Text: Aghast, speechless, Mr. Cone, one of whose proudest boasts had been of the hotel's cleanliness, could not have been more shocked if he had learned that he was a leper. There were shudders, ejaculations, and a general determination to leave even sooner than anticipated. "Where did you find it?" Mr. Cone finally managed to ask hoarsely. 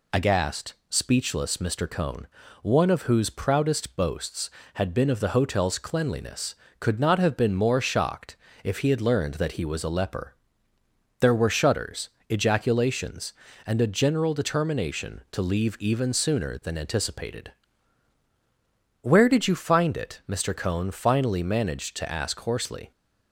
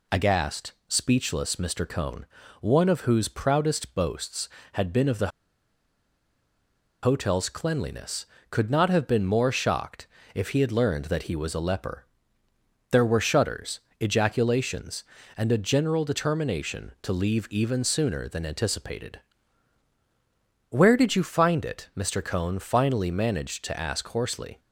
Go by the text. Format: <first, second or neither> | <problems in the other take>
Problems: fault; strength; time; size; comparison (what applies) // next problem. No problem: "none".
first | pauses between "the" and "hotel's"; strong; at 5.2 s; 1.7 s long // pauses between "shocked" and "if"; slight; at 10.0 s; 0.28 s long; slight in the first